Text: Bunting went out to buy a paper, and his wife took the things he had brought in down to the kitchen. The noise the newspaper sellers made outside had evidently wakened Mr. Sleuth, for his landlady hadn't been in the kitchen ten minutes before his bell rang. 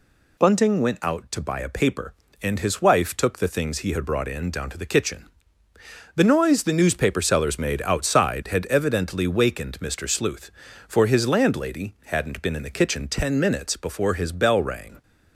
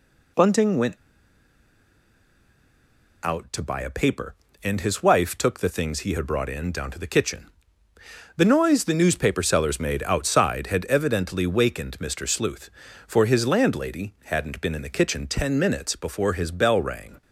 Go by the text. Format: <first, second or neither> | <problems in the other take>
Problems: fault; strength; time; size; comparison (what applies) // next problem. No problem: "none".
first | pauses between "went" and "out"; strong; at 0.9 s; 2.2 s long